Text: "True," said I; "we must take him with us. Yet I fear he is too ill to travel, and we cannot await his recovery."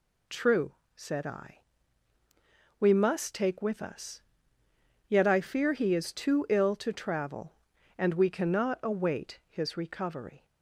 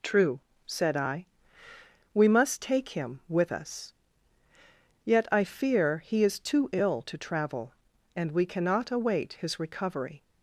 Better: second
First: skips "him"; at 3.6 s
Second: none

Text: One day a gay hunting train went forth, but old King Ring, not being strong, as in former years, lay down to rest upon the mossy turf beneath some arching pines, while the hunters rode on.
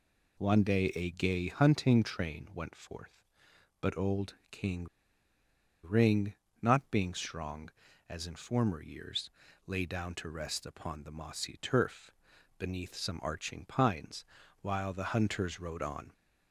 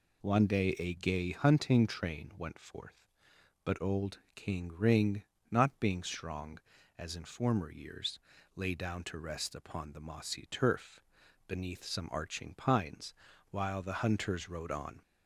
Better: second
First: pauses between "old" and "King"; slight; at 4.3 s; 0.16 s long // pauses between "King" and "Ring"; at 4.8 s; 0.98 s long // pauses between "turf" and "beneath"; noticeable; at 12.1 s; 0.48 s long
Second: pauses between "old" and "King"; slight; at 4.1 s; 0.16 s long // pauses between "turf" and "beneath"; noticeable; at 10.9 s; 0.48 s long

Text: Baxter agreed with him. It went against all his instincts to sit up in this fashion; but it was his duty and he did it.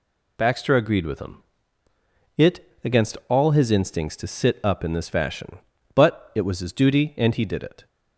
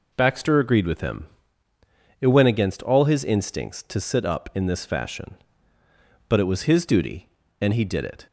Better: second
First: skips "went"; at 2.7 s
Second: none

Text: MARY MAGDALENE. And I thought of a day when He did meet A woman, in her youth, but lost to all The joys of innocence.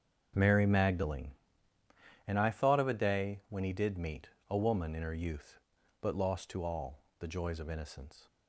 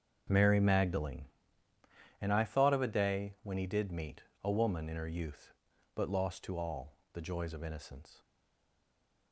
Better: first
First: starts louder than the rest; strong; until 2.3 s; 7.5 dB // pauses between "meet" and "A"; slight; at 4.3 s; 0.20 s long // pauses between "all" and "The"; slight; at 6.9 s; 0.22 s long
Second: starts louder than the rest; strong; until 2.2 s; 7.5 dB // pauses between "meet" and "A"; slight; at 4.2 s; 0.20 s long // pauses between "all" and "The"; slight; at 6.9 s; 0.22 s long // stays silent after the last word; from 8.2 s on; 1.1 s long

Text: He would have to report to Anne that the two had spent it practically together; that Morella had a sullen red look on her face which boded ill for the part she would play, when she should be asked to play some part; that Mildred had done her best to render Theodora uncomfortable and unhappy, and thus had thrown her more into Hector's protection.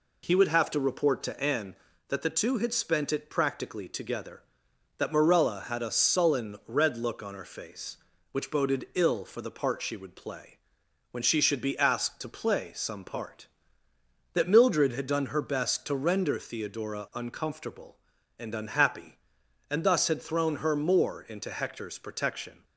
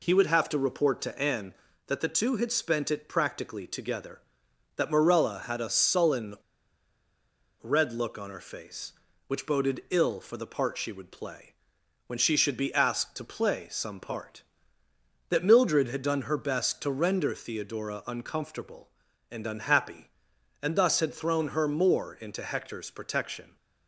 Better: first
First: none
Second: pauses between "sullen" and "red"; strong; at 6.3 s; 1.2 s long

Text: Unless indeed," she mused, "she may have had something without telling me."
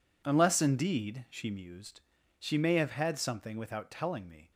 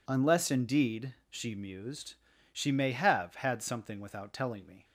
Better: neither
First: none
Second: none

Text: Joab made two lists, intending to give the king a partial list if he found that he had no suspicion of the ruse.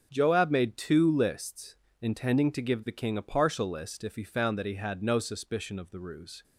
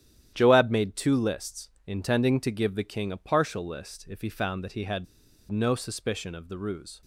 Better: first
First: starts louder than the rest; strong; until 1.1 s; 7 dB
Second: starts louder than the rest; strong; until 1.3 s; 11 dB // pauses between "had" and "no"; at 5.0 s; 0.45 s long

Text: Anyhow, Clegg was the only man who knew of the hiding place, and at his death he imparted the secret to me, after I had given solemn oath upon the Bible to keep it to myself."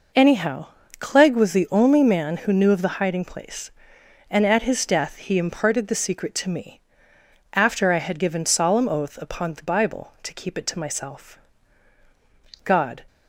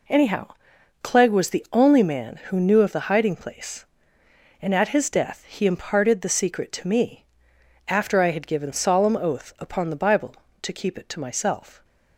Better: second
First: goes on to say "God"; slight; from 12.6 s on; 0.40 s long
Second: none

